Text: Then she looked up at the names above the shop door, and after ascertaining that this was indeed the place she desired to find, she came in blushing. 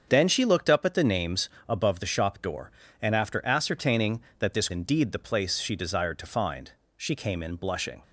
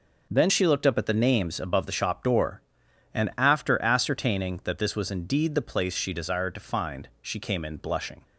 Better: second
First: starts louder than the rest; strong; until 1.0 s; 7 dB // pauses between "names" and "above"; slight; at 1.4 s; 0.18 s long // skips "was"; at 4.7 s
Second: none

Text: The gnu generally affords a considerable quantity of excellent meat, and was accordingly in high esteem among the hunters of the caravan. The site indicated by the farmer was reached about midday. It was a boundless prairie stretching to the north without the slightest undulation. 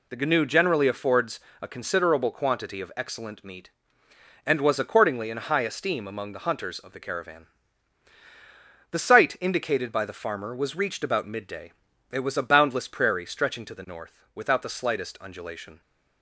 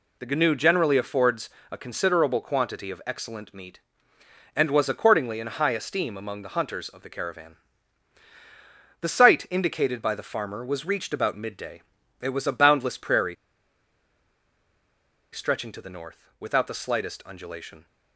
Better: first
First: pauses between "affords" and "a"; slight; at 1.3 s; 0.22 s long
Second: pauses between "affords" and "a"; slight; at 1.4 s; 0.22 s long // pauses between "prairie" and "stretching"; strong; at 13.3 s; 1.9 s long

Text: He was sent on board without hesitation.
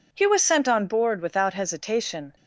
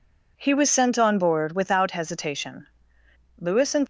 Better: first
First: none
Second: goes on to say "Lewis and"; slight; from 3.3 s on; 0.48 s long

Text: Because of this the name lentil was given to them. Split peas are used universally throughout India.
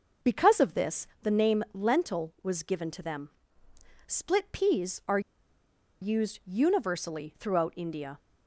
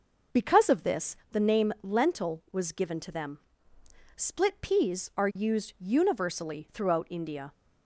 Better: second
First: pauses between "this" and "the"; slight; at 1.0 s; 0.16 s long // pauses between "are" and "used"; noticeable; at 5.1 s; 0.82 s long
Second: pauses between "this" and "the"; slight; at 1.1 s; 0.16 s long

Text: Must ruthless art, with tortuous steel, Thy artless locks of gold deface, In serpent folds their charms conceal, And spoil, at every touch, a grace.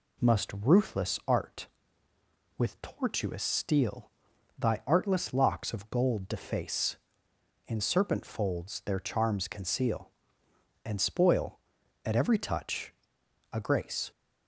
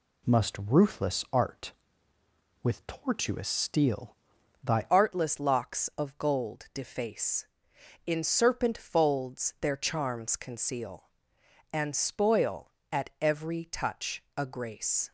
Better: first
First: none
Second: changes voice at "artless"; from 4.8 s on; 10.3 s long

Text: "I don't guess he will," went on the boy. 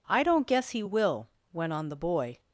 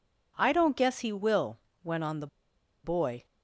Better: first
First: none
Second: pauses between "the" and "boy"; noticeable; at 2.2 s; 0.57 s long

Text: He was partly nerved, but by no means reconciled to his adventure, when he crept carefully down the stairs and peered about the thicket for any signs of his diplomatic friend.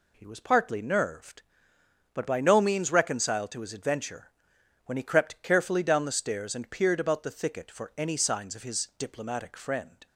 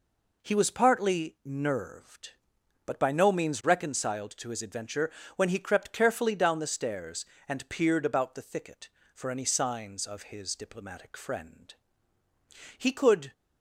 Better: first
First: none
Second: goes on to say "He could"; from 12.7 s on; 0.56 s long

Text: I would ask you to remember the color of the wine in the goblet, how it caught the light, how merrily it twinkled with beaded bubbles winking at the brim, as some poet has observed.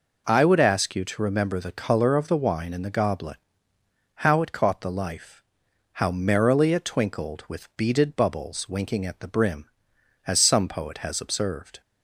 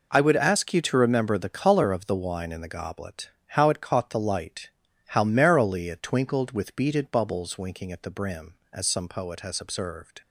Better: second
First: says "life" for "light"; at 4.9 s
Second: none

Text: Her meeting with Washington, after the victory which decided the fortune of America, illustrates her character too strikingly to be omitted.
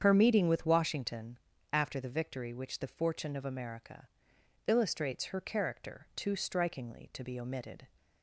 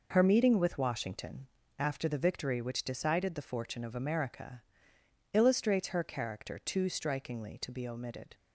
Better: second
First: starts louder than the rest; strong; until 1.0 s; 8 dB // skips "decided"; at 2.8 s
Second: none

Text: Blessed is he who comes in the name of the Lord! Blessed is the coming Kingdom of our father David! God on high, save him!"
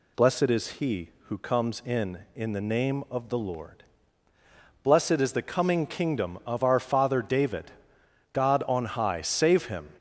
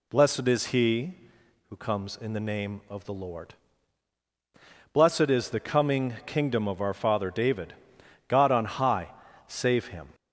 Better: second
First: says "in" twice; at 2.3 s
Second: none

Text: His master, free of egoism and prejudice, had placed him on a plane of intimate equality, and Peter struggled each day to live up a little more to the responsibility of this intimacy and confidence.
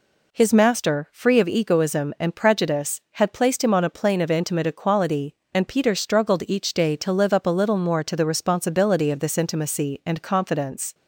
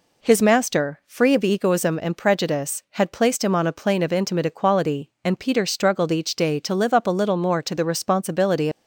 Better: first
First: none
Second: stops before "of this intimacy and confidence"; at 8.7 s

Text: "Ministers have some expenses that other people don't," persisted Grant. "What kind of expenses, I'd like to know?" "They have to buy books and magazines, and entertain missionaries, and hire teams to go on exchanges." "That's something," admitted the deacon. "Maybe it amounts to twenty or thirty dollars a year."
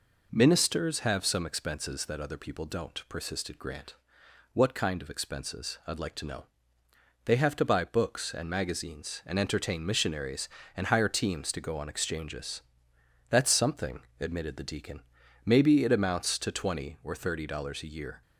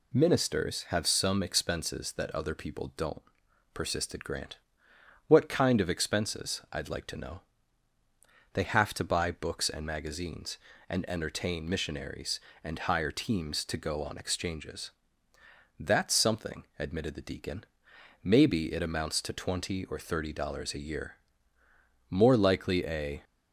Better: first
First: none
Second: goes on to say "More likely a"; noticeable; from 22.0 s on; 1.1 s long

